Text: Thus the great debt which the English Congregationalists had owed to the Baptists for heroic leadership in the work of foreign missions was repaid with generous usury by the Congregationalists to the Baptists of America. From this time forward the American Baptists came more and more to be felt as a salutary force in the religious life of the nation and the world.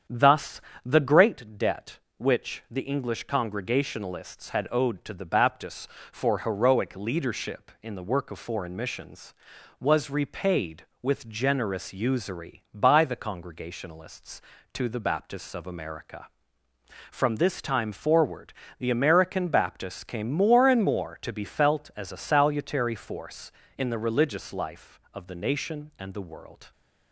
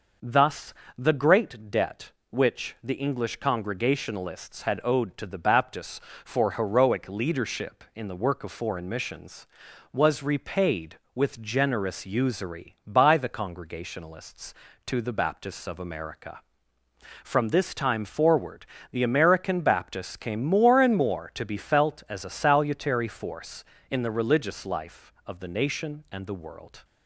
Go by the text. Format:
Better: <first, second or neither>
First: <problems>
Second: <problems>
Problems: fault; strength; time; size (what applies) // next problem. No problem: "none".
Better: second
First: starts louder than the rest; strong; until 1.4 s; 8 dB // pauses between "Thus" and "the"; slight; at 0.6 s; 0.24 s long // pauses between "forward" and "the"; slight; at 18.5 s; 0.24 s long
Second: pauses between "Thus" and "the"; slight; at 0.7 s; 0.24 s long // pauses between "forward" and "the"; slight; at 18.6 s; 0.24 s long